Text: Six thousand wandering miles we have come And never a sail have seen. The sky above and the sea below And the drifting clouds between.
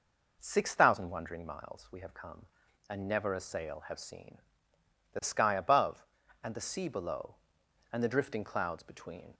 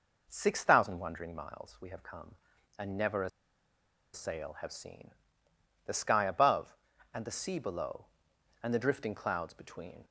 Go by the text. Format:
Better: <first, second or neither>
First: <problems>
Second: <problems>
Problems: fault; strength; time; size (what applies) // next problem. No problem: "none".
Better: first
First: none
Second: pauses between "a" and "sail"; noticeable; at 3.2 s; 0.84 s long